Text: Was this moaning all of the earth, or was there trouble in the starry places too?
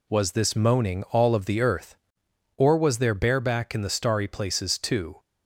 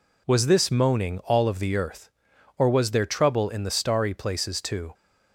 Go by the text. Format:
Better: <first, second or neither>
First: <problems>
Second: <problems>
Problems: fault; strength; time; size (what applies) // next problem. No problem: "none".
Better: second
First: says "bareback" for "trouble"; at 3.1 s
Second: none